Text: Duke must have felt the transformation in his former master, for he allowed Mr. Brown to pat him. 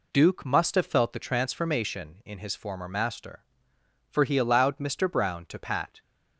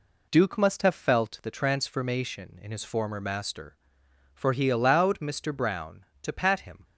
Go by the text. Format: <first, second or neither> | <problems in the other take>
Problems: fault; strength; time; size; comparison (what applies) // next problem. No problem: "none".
second | stops before "him"; at 6.0 s